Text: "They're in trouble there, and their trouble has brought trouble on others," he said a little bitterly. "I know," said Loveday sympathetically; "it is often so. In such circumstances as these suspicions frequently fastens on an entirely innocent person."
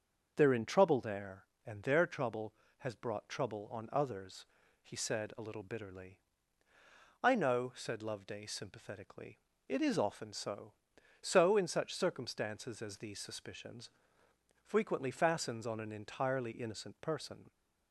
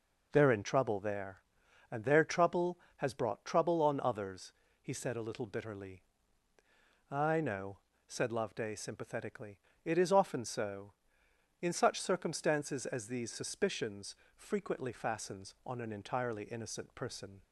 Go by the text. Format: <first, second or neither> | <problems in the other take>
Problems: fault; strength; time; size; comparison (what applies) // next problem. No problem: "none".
second | starts louder than the rest; until 1.3 s; 6.5 dB // says "so" twice; at 11.2 s // pauses between "suspicions" and "frequently"; noticeable; at 13.9 s; 0.72 s long; slight in the second